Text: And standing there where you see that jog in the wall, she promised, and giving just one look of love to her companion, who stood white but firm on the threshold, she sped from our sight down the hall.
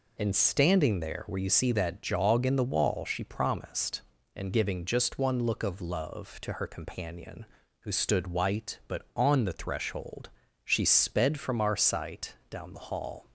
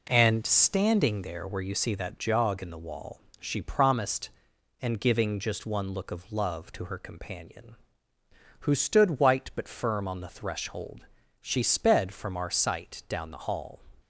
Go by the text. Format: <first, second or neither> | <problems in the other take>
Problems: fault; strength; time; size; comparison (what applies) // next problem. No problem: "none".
second | skips "firm"; at 9.0 s